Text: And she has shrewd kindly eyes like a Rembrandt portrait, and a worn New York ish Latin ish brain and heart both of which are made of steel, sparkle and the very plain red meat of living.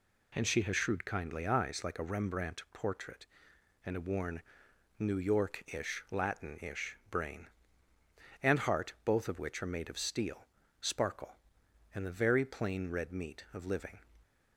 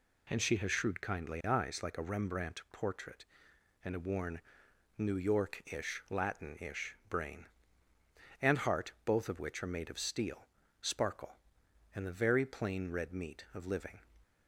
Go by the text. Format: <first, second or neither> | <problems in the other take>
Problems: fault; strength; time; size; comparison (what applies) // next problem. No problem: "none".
neither | pauses between "worn" and "New"; noticeable; the same in both